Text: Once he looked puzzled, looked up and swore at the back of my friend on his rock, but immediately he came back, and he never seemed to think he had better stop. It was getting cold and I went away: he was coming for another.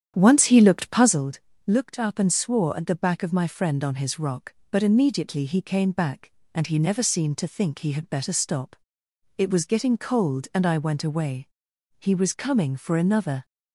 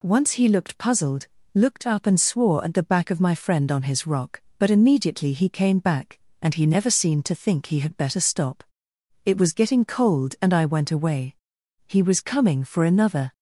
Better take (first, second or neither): second